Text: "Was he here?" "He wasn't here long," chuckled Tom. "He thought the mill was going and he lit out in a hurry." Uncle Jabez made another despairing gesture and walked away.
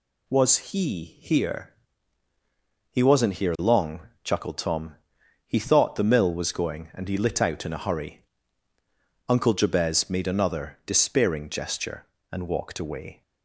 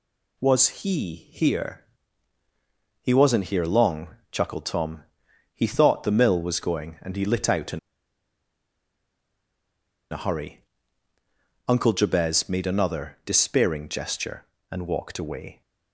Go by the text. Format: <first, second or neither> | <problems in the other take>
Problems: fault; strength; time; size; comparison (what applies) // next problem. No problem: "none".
first | pauses between "in" and "a"; strong; at 7.7 s; 2.3 s long